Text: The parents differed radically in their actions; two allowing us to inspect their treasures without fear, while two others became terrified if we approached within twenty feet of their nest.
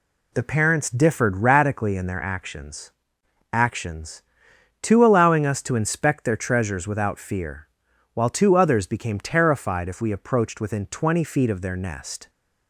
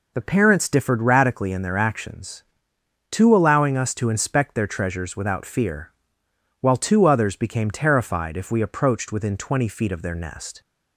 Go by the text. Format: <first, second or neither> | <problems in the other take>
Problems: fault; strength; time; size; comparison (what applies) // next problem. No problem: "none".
second | says "actions" twice; at 3.5 s